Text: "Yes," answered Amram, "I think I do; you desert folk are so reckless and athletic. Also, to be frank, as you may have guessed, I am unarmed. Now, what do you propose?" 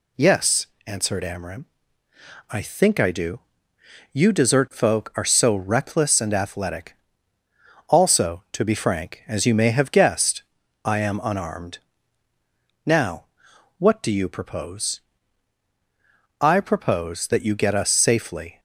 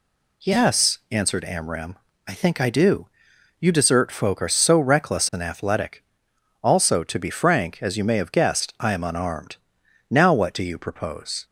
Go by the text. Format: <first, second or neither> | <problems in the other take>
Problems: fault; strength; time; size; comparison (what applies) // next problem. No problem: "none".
second | goes on to say "I propose that you get us safely"; strong; from 16.4 s on; 2.1 s long